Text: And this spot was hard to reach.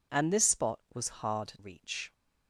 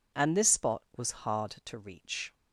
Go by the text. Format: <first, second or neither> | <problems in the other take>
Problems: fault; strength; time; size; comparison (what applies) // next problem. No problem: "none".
second | skips "to"; at 1.5 s